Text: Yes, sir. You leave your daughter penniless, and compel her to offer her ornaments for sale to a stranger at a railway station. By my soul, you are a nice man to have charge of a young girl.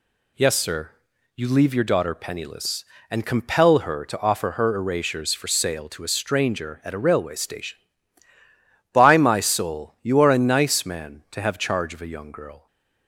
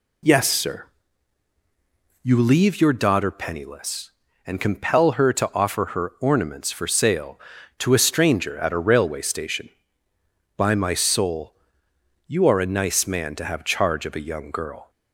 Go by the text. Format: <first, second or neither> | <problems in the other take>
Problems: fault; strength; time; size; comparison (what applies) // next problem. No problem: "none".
second | says "erasures" for "ornaments"; at 4.7 s // stays silent after the last word; slight; from 12.5 s on; 0.5 s long